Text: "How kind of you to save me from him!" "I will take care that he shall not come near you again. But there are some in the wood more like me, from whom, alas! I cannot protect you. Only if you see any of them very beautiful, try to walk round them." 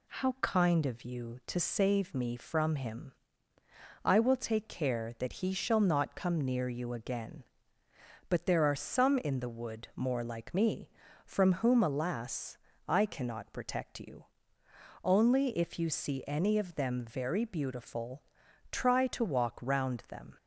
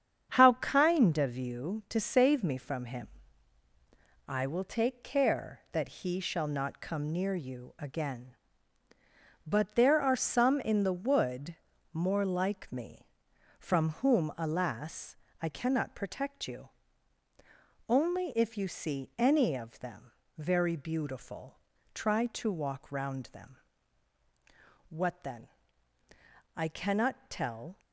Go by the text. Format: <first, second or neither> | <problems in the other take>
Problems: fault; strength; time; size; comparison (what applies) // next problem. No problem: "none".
first | starts louder than the rest; strong; until 1.3 s; 8 dB // pauses between "wood" and "more"; slight; at 11.5 s; 0.36 s long // pauses between "them" and "very"; slight; at 20.1 s; 0.26 s long // goes on to say "What then I cannot tell"; strong; from 24.8 s on; 2.9 s long